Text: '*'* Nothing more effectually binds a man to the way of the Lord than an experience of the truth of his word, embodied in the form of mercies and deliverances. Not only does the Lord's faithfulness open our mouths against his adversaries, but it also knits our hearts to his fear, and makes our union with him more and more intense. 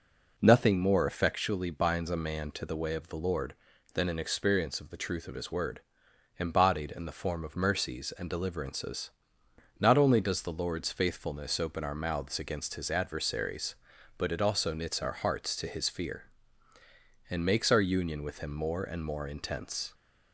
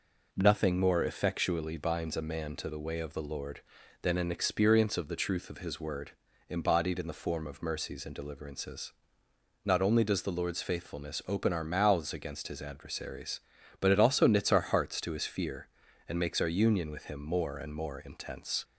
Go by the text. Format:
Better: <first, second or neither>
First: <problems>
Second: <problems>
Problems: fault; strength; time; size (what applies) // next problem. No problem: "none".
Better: neither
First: none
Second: none